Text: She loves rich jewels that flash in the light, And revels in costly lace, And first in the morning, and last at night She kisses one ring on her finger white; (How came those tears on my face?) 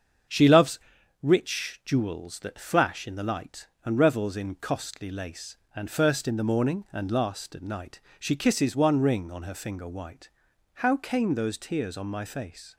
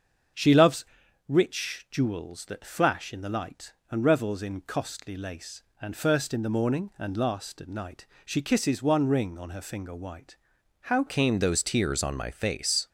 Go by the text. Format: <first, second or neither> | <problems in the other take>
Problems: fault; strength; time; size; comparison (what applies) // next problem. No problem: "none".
first | starts louder than the rest; strong; until 1.7 s; 7 dB; strong in the first // pauses between "loves" and "rich"; at 0.8 s; 0.44 s long; also in the first // pauses between "night" and "She"; slight; at 8.0 s; 0.20 s long; slight in the first // changes voice at "came"; from 11.0 s on; 1.8 s long